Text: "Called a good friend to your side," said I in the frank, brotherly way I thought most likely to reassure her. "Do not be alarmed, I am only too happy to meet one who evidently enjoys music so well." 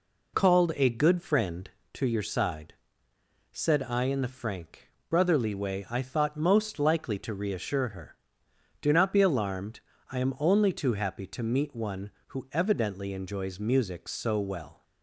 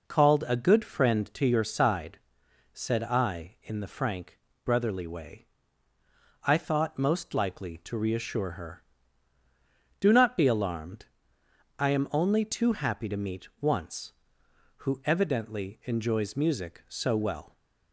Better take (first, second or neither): first